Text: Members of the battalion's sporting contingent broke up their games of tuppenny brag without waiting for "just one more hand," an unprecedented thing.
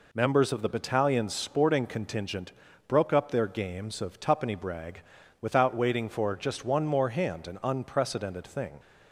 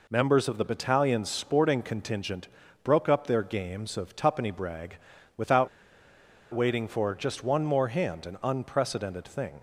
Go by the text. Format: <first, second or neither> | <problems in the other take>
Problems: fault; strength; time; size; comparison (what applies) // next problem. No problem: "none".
first | pauses between "contingent" and "broke"; slight; at 2.4 s; 0.36 s long; slight in the first // pauses between "brag" and "without"; at 4.9 s; 0.38 s long; also in the first // pauses between "without" and "waiting"; noticeable; at 5.6 s; 0.85 s long